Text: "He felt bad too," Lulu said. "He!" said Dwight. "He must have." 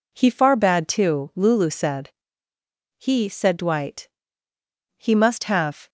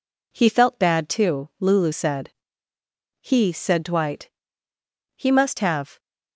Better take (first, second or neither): second